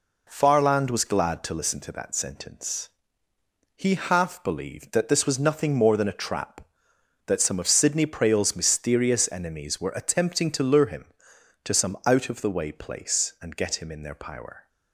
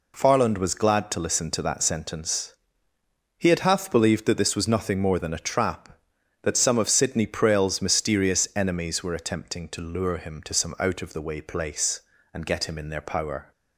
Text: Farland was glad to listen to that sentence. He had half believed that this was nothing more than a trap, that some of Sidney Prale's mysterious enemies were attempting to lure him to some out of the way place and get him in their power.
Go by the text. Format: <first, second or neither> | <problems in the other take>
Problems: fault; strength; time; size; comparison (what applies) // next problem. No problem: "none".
second | skips "had"; at 3.9 s